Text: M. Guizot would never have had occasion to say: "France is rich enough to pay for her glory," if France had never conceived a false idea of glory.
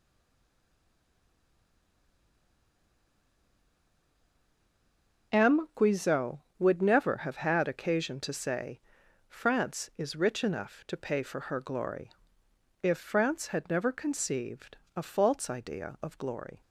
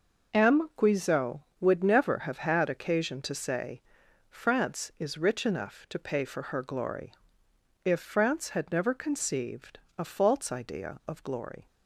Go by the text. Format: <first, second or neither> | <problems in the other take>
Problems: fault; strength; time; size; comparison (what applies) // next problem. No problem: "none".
second | stays silent before the first word; strong; until 5.3 s; 5.3 s long // pauses between "conceived" and "a"; slight; at 14.7 s; 0.18 s long; slight in the second